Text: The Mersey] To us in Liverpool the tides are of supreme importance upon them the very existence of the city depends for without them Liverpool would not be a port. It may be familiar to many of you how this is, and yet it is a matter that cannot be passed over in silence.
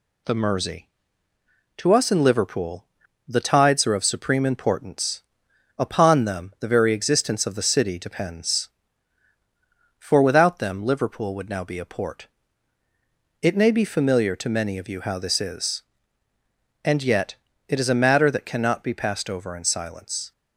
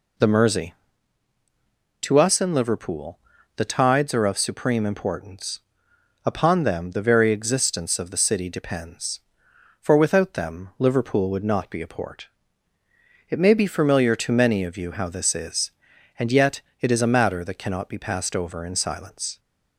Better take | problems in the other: second | pauses between "Liverpool" and "the"; at 2.8 s; 0.42 s long; also in the second // pauses between "importance" and "upon"; noticeable; at 5.2 s; 0.56 s long; noticeable in the second // says "now" for "not"; at 11.4 s // pauses between "yet" and "it"; slight; at 17.3 s; 0.32 s long; slight in the second

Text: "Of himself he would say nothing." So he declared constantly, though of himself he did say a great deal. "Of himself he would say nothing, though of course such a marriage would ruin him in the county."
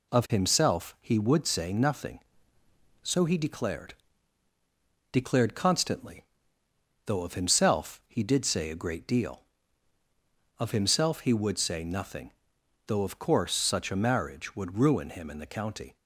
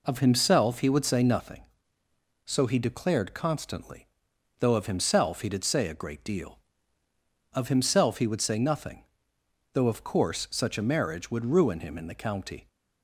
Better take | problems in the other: second | says "declared" twice; at 5.1 s

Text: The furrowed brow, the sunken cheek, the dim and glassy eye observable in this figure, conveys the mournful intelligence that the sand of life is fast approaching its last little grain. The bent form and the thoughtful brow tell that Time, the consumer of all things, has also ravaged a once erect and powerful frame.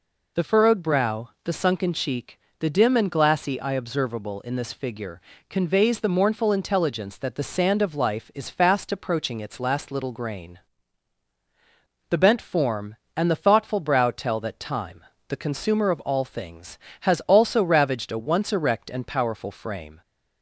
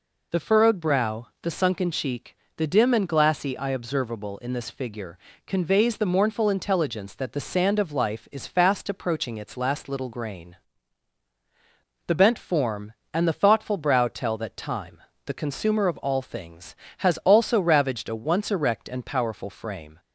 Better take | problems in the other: neither | none

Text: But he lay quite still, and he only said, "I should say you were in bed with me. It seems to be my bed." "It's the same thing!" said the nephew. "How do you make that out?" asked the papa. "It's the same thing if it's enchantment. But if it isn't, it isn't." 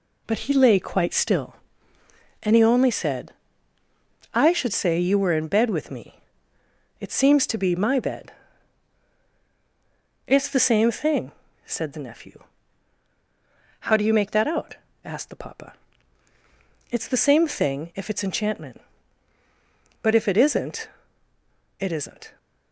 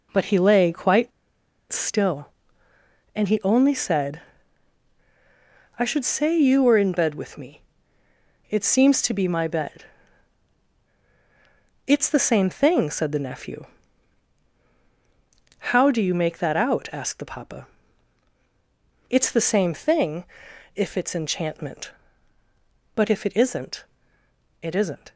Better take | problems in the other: first | pauses between "quite" and "still"; noticeable; at 1.1 s; 0.60 s long // pauses between "thing" and "if"; noticeable; at 20.2 s; 0.50 s long

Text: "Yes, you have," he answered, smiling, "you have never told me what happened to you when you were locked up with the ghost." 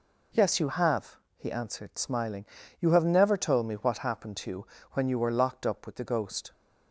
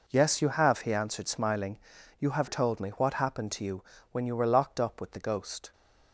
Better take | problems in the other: first | skips "never"; at 2.4 s // pauses between "you" and "when"; slight; at 3.8 s; 0.28 s long; slight in the first

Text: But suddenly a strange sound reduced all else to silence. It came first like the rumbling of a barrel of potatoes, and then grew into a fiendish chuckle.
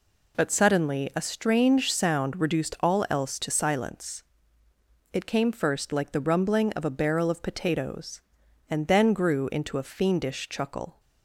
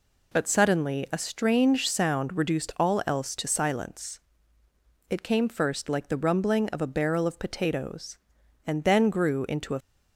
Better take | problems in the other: first | stops before "fiendish chuckle"; at 9.8 s

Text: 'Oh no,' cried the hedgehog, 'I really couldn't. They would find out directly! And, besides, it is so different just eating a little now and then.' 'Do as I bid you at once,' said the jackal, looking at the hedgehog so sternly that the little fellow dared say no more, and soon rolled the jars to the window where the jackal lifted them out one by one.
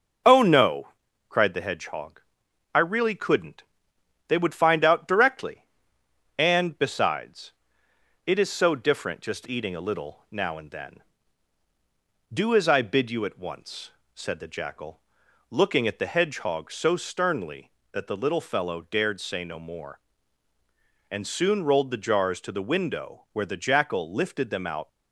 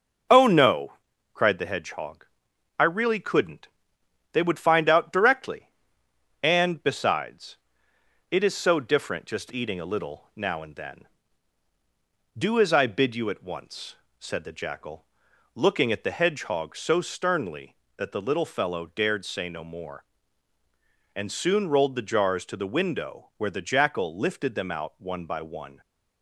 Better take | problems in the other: second | starts louder than the rest; until 1.6 s; 6 dB; noticeable in the second // stops before "one by one"; at 24.8 s

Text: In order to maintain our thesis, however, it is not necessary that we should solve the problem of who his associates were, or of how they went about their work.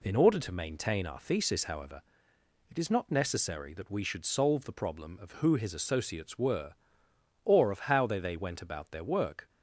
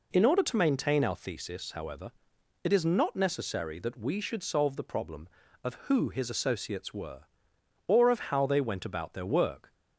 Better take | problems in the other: second | says "they" twice; at 8.1 s

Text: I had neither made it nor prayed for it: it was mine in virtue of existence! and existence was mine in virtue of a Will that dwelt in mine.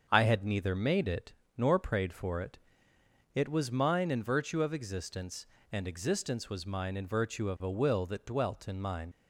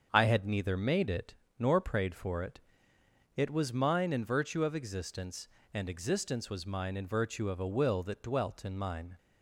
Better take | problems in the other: second | starts louder than the rest; until 1.0 s; 7 dB; also in the second // pauses between "it" and "nor"; slight; at 1.3 s; 0.24 s long; slight in the second // leaves "mine" unfinished; at 9.1 s; 85 ms

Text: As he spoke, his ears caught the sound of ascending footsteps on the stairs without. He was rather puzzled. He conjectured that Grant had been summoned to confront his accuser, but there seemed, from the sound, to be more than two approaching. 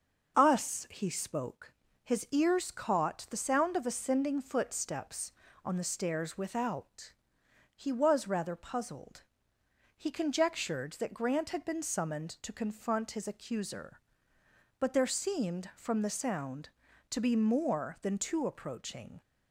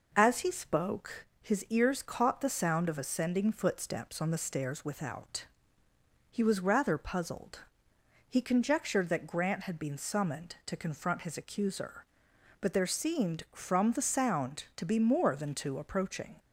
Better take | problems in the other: second | starts louder than the rest; until 1.4 s; 6 dB // says "Us" for "As"; at 0.3 s

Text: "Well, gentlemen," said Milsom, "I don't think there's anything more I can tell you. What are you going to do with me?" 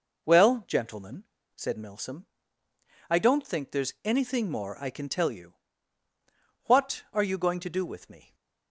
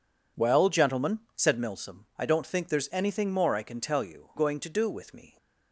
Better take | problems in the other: first | skips "What are you"; at 4.3 s

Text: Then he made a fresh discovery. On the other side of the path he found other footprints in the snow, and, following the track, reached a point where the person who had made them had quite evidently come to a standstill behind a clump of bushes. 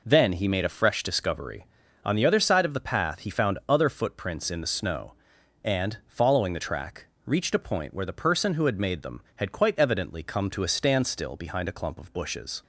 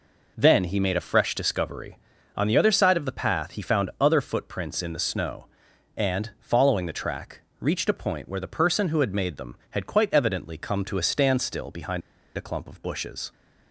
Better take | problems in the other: first | pauses between "behind" and "a"; at 12.0 s; 0.36 s long

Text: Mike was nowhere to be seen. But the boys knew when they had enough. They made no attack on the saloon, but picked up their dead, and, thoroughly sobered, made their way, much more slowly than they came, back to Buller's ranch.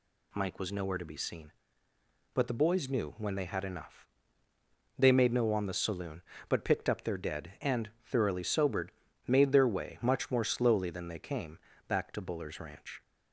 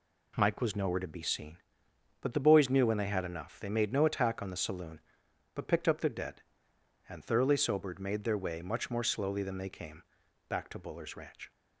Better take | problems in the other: second | skips "attack"; at 5.5 s

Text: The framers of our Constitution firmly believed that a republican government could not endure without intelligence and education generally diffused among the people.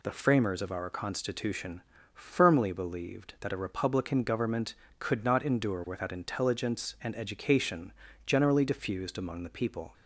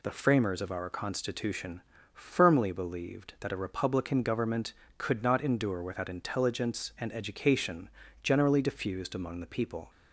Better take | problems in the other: neither | pauses between "Constitution" and "firmly"; slight; the same in both // pauses between "education" and "generally"; slight; the same in both

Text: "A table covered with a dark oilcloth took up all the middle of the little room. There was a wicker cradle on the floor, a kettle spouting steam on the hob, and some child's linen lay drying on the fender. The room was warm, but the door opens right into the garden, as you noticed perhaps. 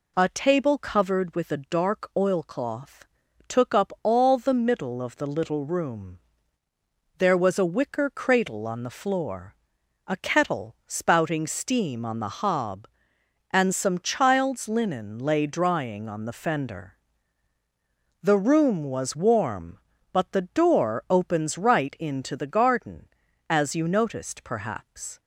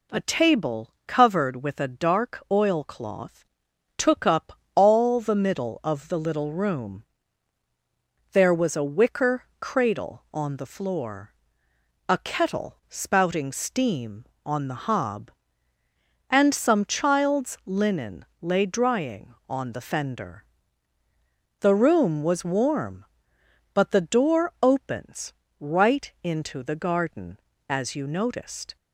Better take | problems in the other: first | pauses between "table" and "covered"; slight; at 0.8 s; 0.16 s long // pauses between "oilcloth" and "took"; noticeable; at 3.4 s; 0.50 s long; also in the first // pauses between "up" and "all"; slight; at 4.5 s; 0.20 s long // pauses between "wicker" and "cradle"; slight; at 9.4 s; 0.16 s long // pauses between "linen" and "lay"; slight; at 18.2 s; 0.16 s long // pauses between "opens" and "right"; slight; at 25.3 s; 0.26 s long // stops before "perhaps"; at 28.7 s

